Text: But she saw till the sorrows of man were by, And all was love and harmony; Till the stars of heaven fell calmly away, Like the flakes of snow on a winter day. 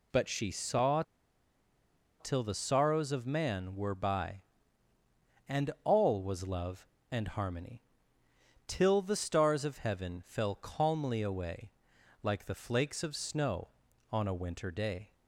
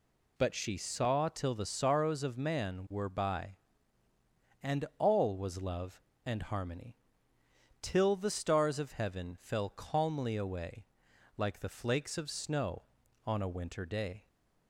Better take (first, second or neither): second